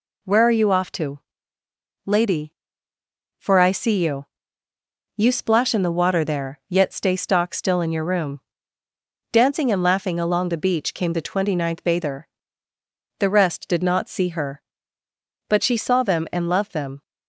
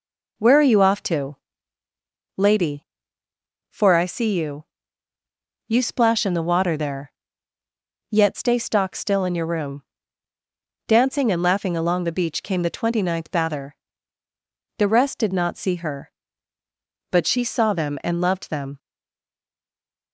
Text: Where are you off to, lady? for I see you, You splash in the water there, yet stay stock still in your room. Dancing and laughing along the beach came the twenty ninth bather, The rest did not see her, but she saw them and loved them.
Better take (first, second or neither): first